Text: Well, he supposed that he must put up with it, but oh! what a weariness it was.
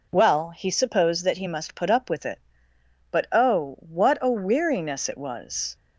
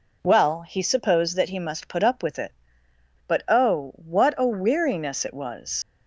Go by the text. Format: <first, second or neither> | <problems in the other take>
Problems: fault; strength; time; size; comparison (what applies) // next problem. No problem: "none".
first | leaves "was" unfinished; at 5.8 s; 90 ms